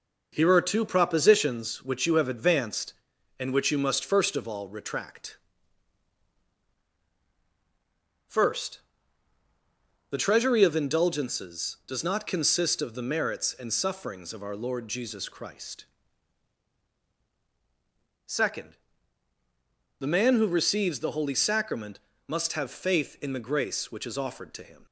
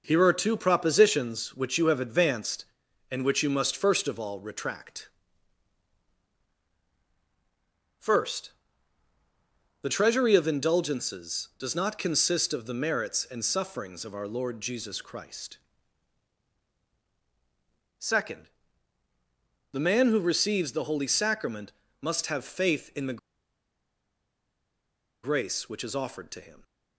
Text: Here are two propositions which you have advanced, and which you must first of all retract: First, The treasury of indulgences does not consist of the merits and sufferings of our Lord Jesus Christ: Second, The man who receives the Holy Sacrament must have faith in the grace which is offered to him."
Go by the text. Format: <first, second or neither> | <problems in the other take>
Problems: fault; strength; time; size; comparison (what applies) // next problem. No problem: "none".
first | pauses between "Sacrament" and "must"; slight; at 21.7 s; 0.28 s long; slight in the first // pauses between "the" and "grace"; strong; at 23.1 s; 2.0 s long